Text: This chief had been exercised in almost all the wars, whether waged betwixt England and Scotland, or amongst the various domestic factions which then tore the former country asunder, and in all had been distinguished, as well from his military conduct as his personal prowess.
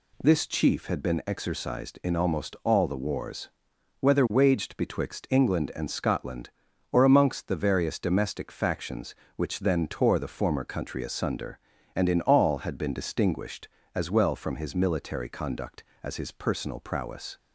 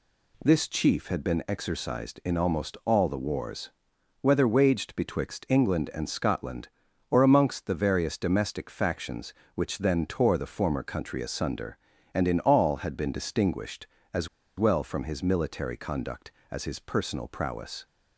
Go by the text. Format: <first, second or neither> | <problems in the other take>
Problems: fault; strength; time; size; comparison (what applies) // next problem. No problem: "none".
first | pauses between "as" and "well"; slight; at 14.2 s; 0.30 s long